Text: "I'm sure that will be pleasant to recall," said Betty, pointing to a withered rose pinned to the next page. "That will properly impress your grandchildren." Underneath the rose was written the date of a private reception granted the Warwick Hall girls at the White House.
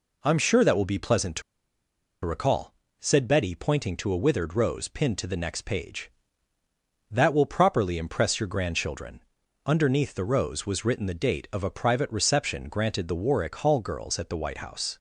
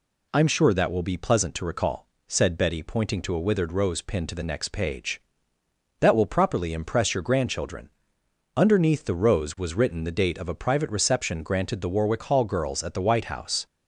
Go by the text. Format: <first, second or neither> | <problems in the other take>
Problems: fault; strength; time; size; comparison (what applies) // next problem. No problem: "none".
second | pauses between "to" and "recall"; noticeable; at 1.4 s; 0.83 s long